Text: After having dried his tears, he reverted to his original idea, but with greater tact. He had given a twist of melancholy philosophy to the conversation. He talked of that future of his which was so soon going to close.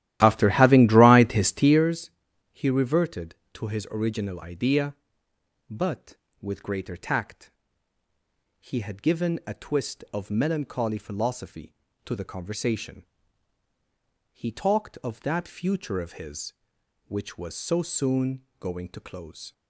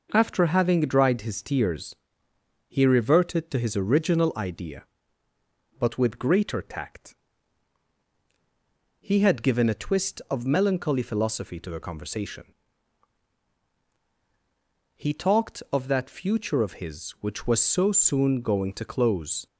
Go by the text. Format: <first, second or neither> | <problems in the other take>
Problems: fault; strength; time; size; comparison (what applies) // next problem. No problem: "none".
second | starts louder than the rest; strong; until 1.9 s; 14 dB // pauses between "soon" and "going"; slight; at 18.4 s; 0.18 s long